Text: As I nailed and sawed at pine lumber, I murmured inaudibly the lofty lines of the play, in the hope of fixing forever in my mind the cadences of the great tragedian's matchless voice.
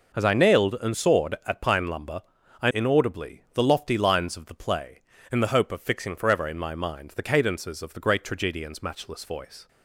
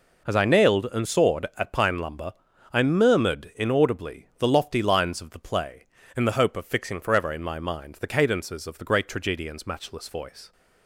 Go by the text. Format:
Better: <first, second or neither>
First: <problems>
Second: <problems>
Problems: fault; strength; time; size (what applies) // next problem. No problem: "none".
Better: second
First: skips "murmured"; at 2.7 s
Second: none